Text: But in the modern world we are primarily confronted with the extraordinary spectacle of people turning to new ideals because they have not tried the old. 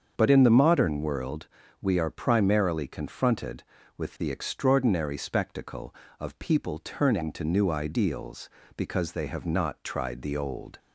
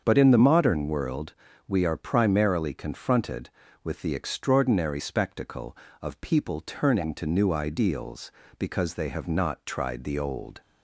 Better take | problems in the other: neither | starts louder than the rest; the same in both // pauses between "world" and "we"; slight; the same in both

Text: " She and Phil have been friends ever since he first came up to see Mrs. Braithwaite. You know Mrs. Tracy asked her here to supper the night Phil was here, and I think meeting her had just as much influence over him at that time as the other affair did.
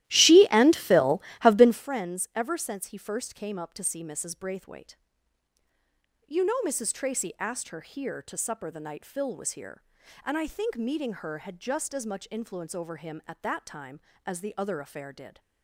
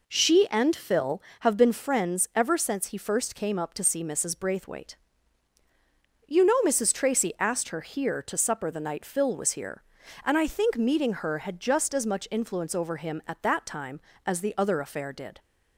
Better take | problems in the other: second | starts louder than the rest; strong; until 1.9 s; 14.5 dB

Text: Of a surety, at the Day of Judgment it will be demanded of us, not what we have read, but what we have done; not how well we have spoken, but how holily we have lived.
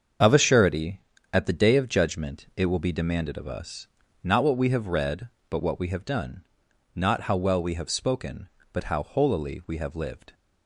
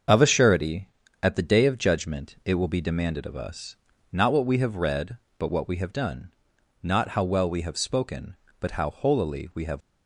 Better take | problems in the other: first | starts louder than the rest; until 1.4 s; 7 dB; also in the first // stops before "lived"; at 9.8 s

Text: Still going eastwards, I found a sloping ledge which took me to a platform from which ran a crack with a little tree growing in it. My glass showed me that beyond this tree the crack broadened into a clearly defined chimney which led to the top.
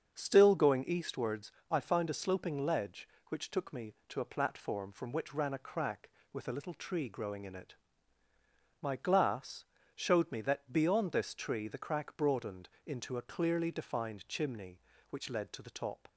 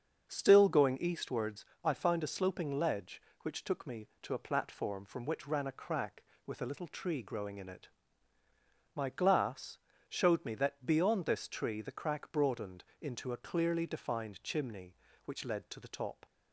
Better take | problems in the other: neither | starts louder than the rest; the same in both // pauses between "glass" and "showed"; slight; the same in both // pauses between "broadened" and "into"; slight; the same in both

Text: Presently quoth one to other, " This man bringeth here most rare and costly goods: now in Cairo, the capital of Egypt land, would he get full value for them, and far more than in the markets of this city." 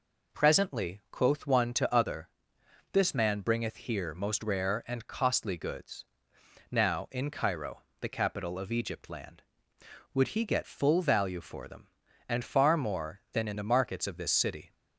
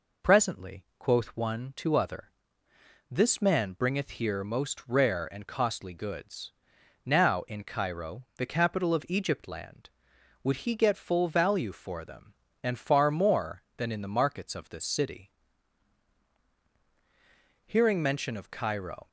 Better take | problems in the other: first | goes on to say "Hearing mention of Cairo"; from 17.6 s on; 1.4 s long

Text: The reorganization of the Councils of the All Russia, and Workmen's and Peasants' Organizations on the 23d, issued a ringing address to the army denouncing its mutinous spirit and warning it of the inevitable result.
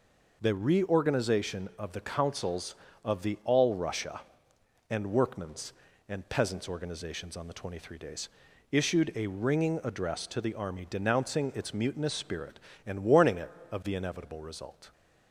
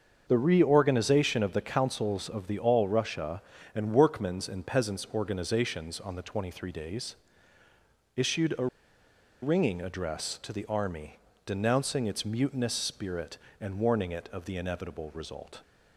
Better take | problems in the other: first | starts louder than the rest; until 1.2 s; 6.5 dB // pauses between "a" and "ringing"; noticeable; at 8.6 s; 0.76 s long // pauses between "army" and "denouncing"; slight; at 11.1 s; 0.30 s long

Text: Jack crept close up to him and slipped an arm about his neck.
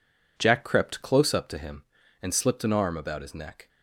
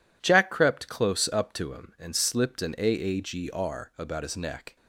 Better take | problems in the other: first | says "aagr" for "arm"; at 2.7 s

